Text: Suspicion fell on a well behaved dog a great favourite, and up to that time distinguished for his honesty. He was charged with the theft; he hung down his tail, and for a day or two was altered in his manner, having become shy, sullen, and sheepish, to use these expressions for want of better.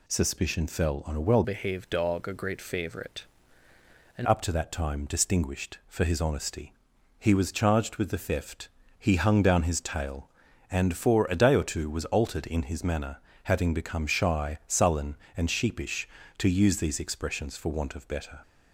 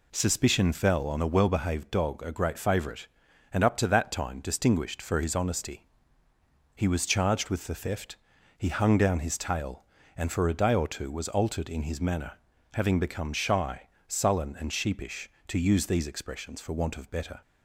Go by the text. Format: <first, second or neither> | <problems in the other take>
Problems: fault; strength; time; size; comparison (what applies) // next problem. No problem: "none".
second | changes voice from "behaved" to "and"; from 1.4 to 4.2 s; 2.8 s long